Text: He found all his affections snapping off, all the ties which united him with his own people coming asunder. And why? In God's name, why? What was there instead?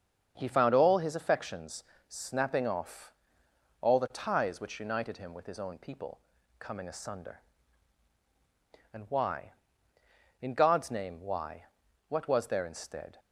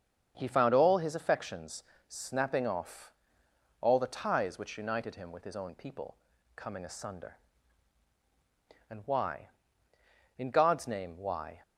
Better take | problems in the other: first | starts louder than the rest; strong; until 1.3 s; 7 dB; also in the first // pauses between "affections" and "snapping"; slight; at 1.8 s; 0.26 s long; slight in the first // pauses between "people" and "coming"; at 6.1 s; 0.40 s long; also in the first // stops before "What was there instead"; at 11.6 s

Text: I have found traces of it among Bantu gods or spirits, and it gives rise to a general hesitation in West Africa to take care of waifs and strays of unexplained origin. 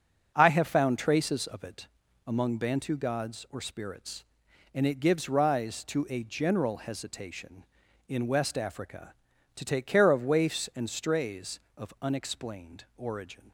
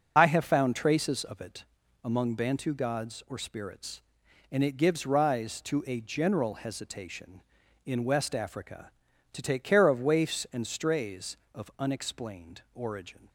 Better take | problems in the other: first | loses the start of "I"; at 0.1 s; 40 ms // starts louder than the rest; until 1.1 s; 6.5 dB; also in the first // pauses between "it" and "among"; at 1.6 s; 0.38 s long; also in the first

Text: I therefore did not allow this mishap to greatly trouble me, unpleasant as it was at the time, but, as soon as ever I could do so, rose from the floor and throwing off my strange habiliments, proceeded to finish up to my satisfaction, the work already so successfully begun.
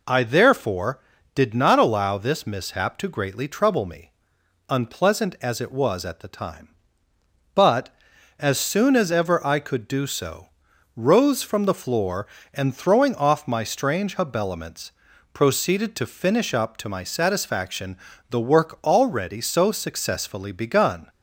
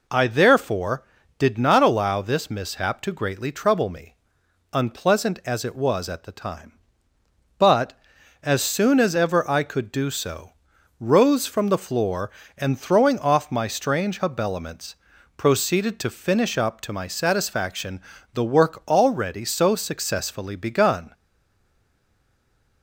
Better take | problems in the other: first | stays silent after the last word; noticeable; from 21.1 s on; 1.7 s long

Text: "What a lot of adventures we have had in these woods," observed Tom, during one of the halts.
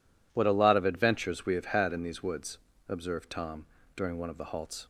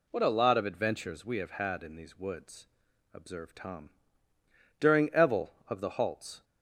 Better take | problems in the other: first | says "evel" for "one"; at 5.0 s

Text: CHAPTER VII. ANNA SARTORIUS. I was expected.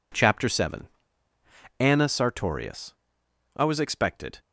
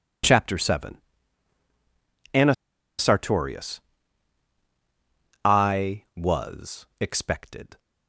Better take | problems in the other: first | pauses between "ANNA" and "SARTORIUS"; noticeable; at 2.5 s; 0.46 s long // pauses between "was" and "expected"; slight; at 6.8 s; 0.16 s long

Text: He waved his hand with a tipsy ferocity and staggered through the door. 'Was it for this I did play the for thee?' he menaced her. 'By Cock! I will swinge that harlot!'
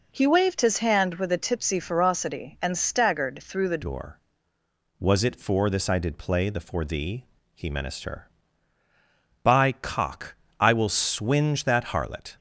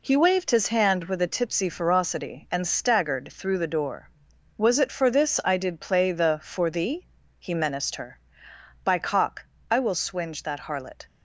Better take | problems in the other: second | changes voice at "door"; from 3.8 s on; 8.5 s long

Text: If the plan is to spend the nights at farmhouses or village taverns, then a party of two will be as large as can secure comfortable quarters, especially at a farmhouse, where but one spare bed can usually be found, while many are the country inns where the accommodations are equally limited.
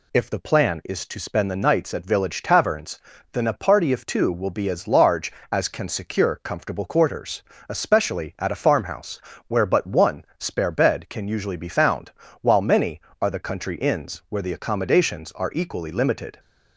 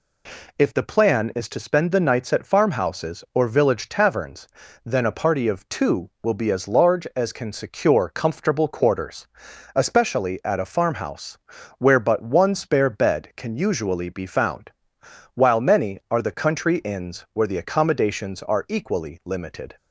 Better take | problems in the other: second | skips "farmhouses or"; at 2.0 s

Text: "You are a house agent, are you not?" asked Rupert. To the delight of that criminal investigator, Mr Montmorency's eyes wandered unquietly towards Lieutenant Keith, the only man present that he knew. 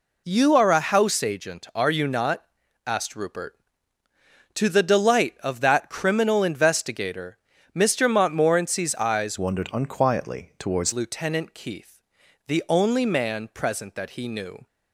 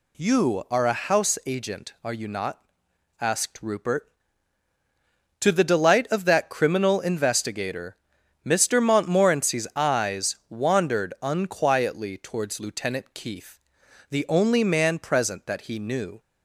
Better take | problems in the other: second | changes voice from "wandered" to "towards"; from 9.3 to 10.9 s; 1.6 s long

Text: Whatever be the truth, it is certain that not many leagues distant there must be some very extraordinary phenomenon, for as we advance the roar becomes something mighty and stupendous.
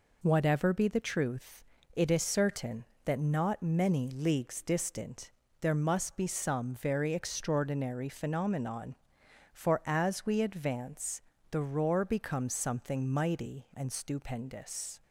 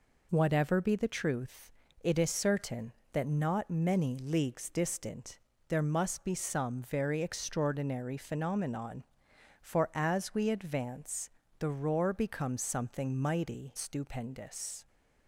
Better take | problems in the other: first | pauses between "distant" and "there"; slight; at 5.3 s; 0.30 s long; slight in the first // pauses between "advance" and "the"; slight; at 11.2 s; 0.28 s long; slight in the first // skips "and"; at 13.7 s

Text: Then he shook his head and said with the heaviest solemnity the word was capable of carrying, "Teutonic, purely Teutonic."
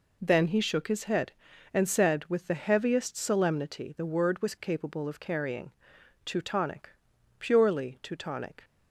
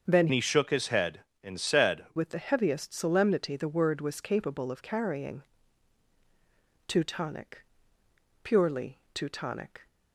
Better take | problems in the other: first | starts louder than the rest; until 1.1 s; 7 dB // changes voice from "he" to "said"; from 0.3 to 2.0 s; 1.7 s long // pauses between "purely" and "Teutonic"; slight; at 8.9 s; 0.16 s long

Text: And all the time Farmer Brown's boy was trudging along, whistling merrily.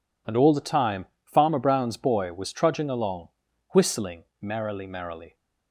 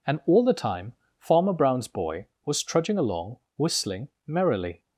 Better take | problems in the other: second | pauses between "time" and "Farmer"; slight; at 1.0 s; 0.20 s long; slight in the second // pauses between "whistling" and "merrily"; slight; at 4.2 s; 0.18 s long; slight in the second // says "merrily" twice; at 4.8 s

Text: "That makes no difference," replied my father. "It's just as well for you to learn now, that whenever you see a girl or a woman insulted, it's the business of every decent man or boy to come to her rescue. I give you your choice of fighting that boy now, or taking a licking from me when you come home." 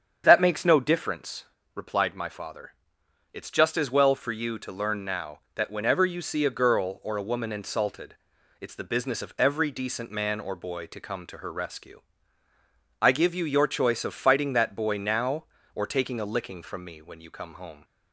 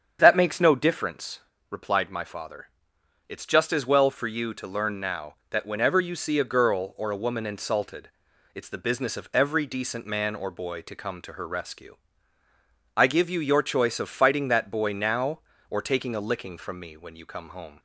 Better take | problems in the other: neither | starts louder than the rest; strong; the same in both

